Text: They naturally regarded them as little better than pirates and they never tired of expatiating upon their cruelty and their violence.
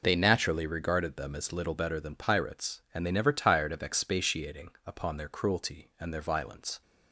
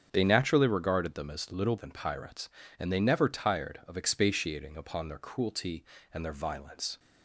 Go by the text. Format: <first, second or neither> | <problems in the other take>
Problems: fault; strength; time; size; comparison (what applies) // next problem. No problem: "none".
first | starts louder than the rest; strong; until 1.1 s; 7 dB // skips "better"; at 1.7 s